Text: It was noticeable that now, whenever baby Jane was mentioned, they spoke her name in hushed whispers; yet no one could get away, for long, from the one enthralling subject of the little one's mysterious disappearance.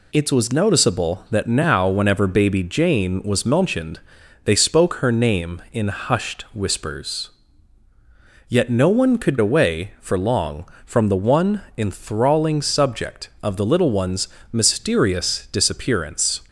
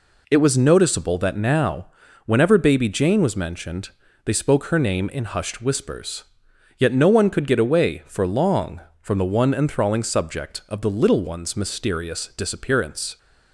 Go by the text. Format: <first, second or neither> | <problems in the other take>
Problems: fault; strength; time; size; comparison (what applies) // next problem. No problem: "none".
second | skips "get"; at 9.3 s // pauses between "one" and "enthralling"; slight; at 11.6 s; 0.16 s long // pauses between "one's" and "mysterious"; slight; at 14.2 s; 0.24 s long